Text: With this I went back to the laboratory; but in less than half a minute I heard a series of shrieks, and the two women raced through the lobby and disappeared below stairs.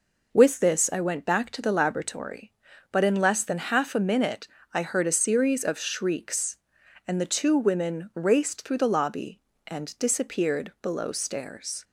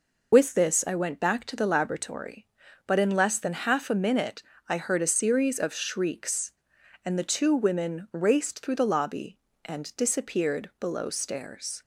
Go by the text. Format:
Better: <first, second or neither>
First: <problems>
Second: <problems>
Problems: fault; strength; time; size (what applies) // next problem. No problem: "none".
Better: first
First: pauses between "minute" and "I"; slight; at 4.4 s; 0.24 s long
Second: loses the start of "With"; at 0.3 s; 60 ms // pauses between "minute" and "I"; slight; at 4.4 s; 0.24 s long